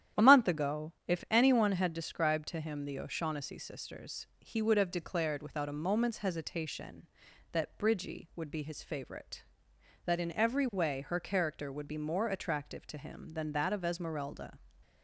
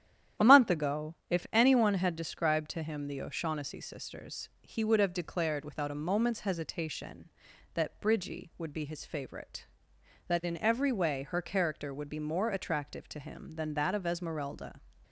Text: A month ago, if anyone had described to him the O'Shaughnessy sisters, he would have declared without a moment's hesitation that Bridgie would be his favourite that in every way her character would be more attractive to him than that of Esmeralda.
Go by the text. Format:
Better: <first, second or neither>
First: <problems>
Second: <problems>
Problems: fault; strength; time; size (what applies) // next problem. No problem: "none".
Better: neither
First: starts louder than the rest; strong; until 1.3 s; 10.5 dB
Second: starts louder than the rest; strong; until 1.5 s; 10.5 dB